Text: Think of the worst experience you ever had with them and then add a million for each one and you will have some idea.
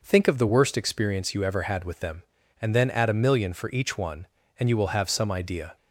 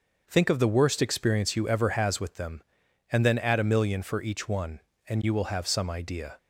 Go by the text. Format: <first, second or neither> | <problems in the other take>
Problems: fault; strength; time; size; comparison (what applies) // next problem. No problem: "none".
first | starts louder than the rest; until 1.2 s; 6.5 dB // says "has" for "had"; at 1.8 s